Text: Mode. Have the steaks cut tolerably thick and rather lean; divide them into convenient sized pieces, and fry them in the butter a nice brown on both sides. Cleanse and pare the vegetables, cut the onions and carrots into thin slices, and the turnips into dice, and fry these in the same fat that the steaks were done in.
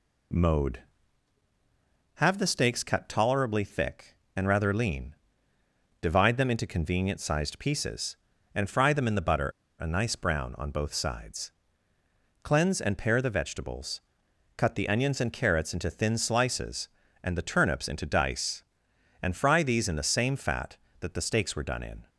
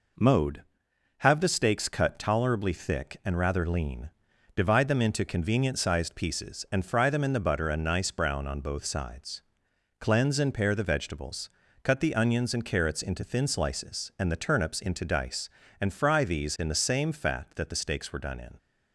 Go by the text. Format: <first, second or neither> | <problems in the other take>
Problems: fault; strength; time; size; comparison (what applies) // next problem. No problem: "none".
second | pauses between "butter" and "a"; slight; at 9.5 s; 0.28 s long